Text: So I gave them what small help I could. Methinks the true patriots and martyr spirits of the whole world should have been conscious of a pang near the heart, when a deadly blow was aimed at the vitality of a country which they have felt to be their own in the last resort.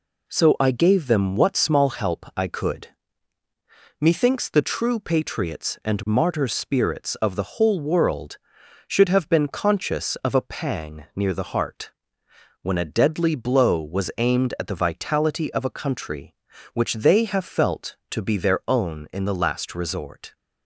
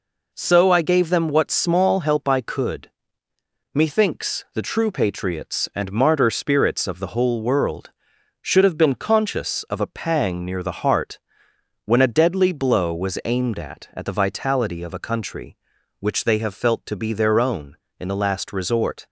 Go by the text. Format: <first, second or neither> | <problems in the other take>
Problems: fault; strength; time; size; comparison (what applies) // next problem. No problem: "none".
first | says "at" twice; at 13.9 s